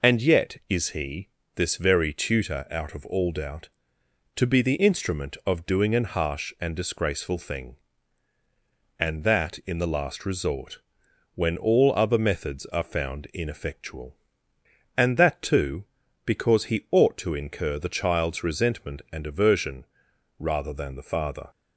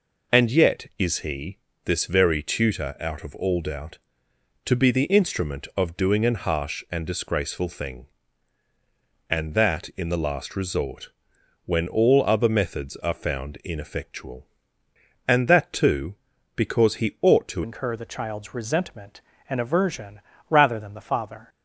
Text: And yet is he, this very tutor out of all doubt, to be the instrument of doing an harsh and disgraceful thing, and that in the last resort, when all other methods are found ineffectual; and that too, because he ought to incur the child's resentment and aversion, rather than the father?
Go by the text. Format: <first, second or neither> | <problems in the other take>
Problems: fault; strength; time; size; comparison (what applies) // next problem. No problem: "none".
first | changes voice at "incur"; from 17.6 s on; 3.8 s long